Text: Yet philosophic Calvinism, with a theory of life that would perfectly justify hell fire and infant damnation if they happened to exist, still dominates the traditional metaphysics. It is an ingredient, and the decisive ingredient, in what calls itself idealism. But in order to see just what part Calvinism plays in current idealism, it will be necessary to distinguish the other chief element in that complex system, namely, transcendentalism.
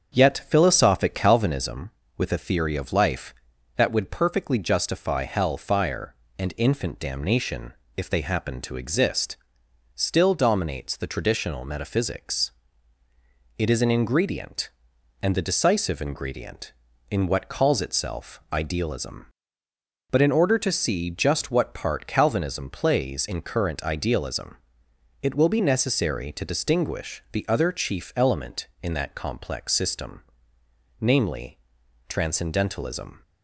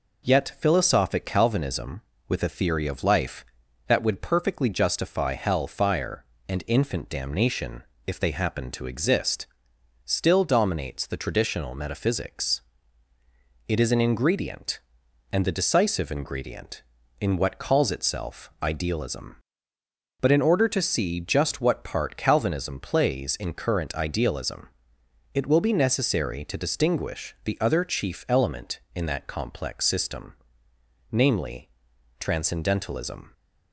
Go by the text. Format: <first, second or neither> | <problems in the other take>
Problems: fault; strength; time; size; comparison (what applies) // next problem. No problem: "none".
second | starts louder than the rest; strong; until 1.7 s; 7.5 dB // pauses between "damnation" and "if"; slight; at 7.7 s; 0.24 s long; slight in the second